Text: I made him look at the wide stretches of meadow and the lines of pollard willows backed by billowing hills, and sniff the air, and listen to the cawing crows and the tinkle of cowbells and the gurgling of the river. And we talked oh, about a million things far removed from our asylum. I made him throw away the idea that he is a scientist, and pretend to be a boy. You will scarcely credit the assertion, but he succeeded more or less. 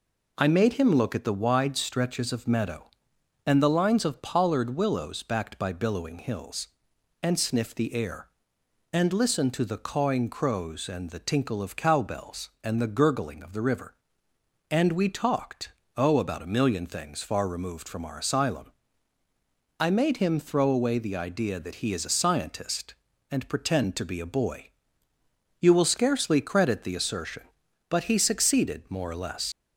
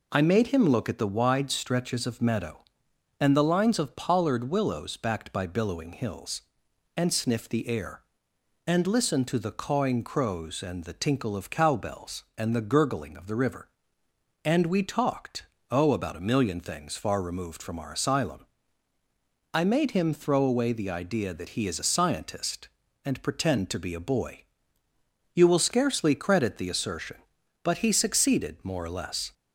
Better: second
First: pauses between "talked" and "oh"; slight; at 15.6 s; 0.26 s long // leaves "less" unfinished; at 29.5 s; 70 ms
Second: pauses between "talked" and "oh"; slight; at 15.4 s; 0.26 s long

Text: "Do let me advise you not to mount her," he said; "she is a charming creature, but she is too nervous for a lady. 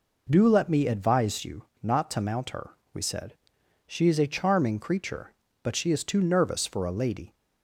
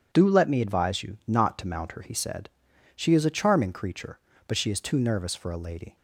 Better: second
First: pauses between "you" and "not"; slight; at 1.6 s; 0.18 s long // says "we" for "he"; at 2.9 s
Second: none

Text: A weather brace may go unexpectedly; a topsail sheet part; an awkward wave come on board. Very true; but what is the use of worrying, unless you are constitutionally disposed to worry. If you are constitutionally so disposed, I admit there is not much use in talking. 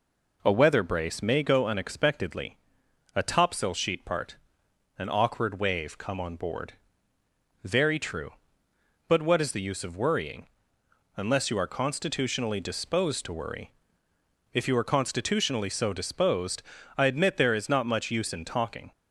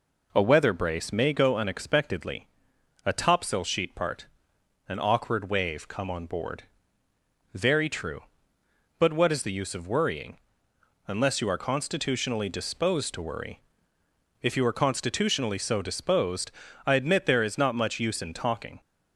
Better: neither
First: none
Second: none

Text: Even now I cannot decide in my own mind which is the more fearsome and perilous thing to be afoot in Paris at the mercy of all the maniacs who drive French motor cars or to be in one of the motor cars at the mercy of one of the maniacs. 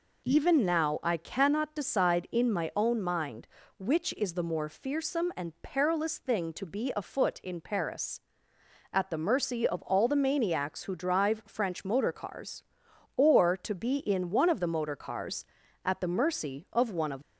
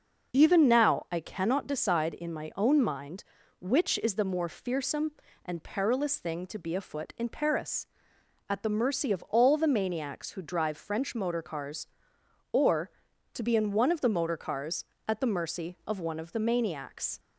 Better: second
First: stops before "the maniacs"; at 17.2 s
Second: none

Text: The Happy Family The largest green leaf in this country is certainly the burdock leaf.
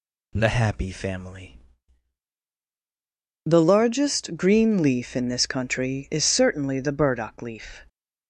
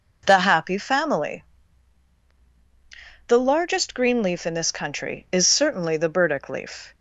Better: neither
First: pauses between "Family" and "The"; strong; at 1.5 s; 1.8 s long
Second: pauses between "Family" and "The"; strong; at 1.4 s; 1.8 s long

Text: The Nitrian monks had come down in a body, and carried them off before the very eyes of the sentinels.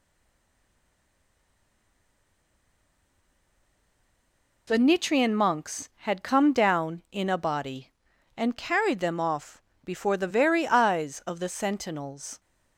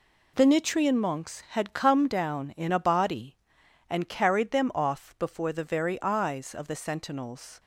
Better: second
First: stays silent before the first word; strong; until 4.6 s; 4.6 s long // pauses between "off" and "before"; slight; at 9.6 s; 0.20 s long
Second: none

